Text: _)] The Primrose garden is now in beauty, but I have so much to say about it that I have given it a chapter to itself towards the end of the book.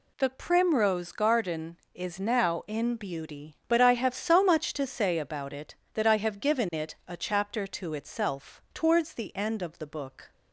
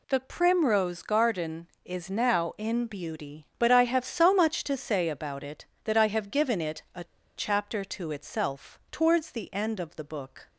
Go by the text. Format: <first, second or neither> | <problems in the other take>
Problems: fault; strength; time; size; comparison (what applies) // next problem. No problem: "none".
first | pauses between "a" and "chapter"; slight; at 7.0 s; 0.32 s long